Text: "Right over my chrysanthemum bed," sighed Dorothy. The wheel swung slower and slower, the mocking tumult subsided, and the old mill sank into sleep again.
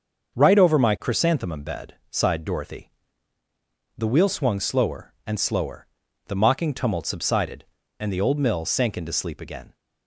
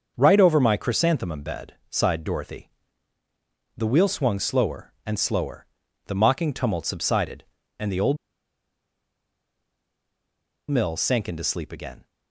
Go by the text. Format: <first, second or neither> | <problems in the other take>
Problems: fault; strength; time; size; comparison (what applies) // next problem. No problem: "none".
first | starts louder than the rest; until 1.1 s; 6.5 dB; also in the first // pauses between "old" and "mill"; strong; at 8.1 s; 2.5 s long